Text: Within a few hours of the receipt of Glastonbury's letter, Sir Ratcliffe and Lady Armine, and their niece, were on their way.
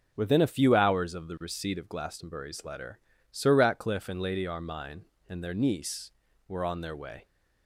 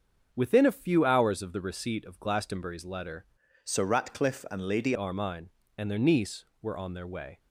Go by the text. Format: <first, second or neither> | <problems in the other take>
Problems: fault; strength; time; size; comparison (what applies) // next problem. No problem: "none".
first | starts louder than the rest; until 1.3 s; 7 dB; noticeable in the first // changes voice from "Sir" to "Lady"; from 3.6 to 4.9 s; 1.3 s long